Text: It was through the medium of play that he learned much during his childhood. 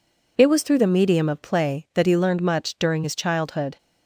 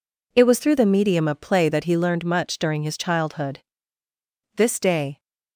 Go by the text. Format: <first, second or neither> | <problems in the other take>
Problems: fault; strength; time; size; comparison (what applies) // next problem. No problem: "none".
first | goes on to say "This day"; noticeable; from 4.5 s on; 0.64 s long